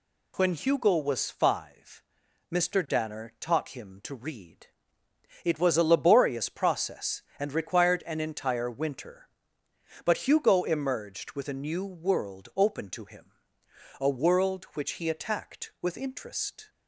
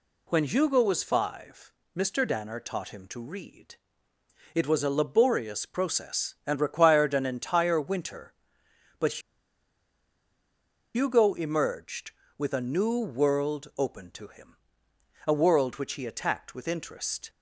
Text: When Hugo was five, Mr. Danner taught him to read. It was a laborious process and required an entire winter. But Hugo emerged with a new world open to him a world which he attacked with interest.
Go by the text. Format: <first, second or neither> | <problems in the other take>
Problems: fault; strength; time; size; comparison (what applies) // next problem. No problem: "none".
first | pauses between "But" and "Hugo"; strong; at 9.2 s; 1.7 s long // pauses between "him" and "a"; noticeable; at 14.5 s; 0.72 s long; noticeable in the first